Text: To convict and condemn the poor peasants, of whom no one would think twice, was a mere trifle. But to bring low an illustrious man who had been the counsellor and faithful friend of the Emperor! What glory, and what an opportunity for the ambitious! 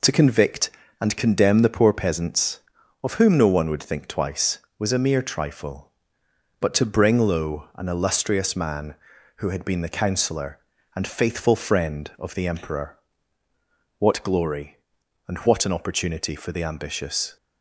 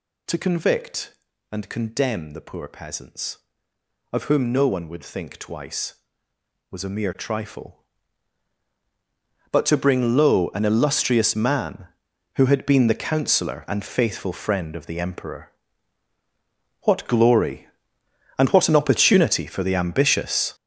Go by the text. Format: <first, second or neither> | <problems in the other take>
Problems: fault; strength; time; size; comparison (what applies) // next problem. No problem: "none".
first | gets louder; strong; throughout; 9 dB